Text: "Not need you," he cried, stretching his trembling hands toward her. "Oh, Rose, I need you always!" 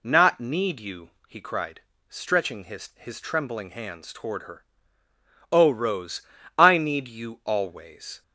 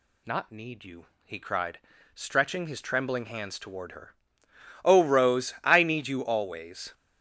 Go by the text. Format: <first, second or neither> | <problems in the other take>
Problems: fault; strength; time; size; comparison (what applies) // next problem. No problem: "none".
second | says "his" twice; at 2.9 s